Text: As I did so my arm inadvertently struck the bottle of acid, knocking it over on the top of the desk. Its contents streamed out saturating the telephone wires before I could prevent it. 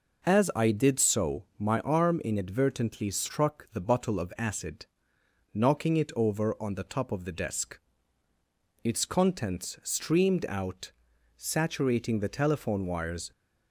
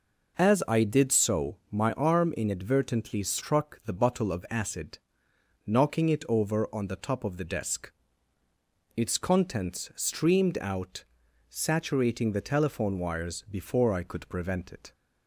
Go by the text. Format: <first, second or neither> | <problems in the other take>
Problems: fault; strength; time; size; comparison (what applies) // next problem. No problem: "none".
second | pauses between "out" and "saturating"; noticeable; at 10.9 s; 0.50 s long; noticeable in the second // stops before "before I could prevent it"; at 13.3 s